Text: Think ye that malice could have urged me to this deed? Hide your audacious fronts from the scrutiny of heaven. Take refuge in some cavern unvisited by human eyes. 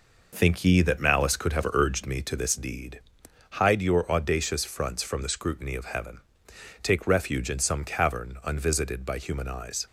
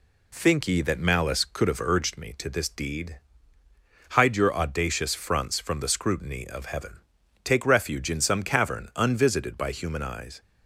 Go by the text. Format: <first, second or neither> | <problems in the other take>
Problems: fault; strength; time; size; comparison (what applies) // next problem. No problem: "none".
second | starts louder than the rest; noticeable; until 2.2 s; 5 dB